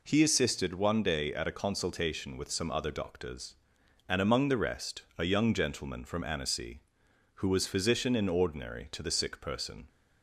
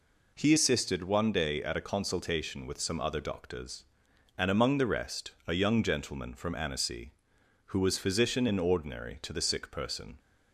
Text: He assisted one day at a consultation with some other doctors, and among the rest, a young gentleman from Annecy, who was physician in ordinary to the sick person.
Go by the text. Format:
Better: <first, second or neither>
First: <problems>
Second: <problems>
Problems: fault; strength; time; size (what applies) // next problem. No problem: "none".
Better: neither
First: none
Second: none